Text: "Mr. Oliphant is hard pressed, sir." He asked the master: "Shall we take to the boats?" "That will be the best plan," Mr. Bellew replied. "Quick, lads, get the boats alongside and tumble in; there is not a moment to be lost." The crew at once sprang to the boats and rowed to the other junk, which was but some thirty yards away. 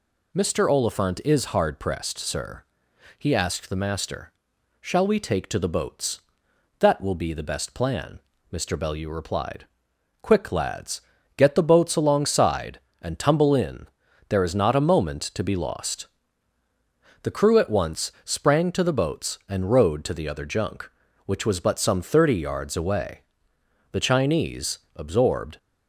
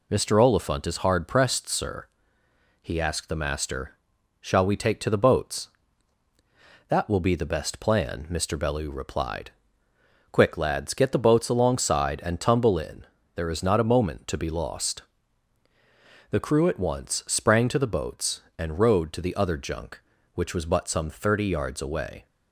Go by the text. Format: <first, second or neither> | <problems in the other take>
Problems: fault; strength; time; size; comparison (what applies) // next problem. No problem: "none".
second | goes on to say "The Chinese absorbed"; from 23.9 s on; 1.6 s long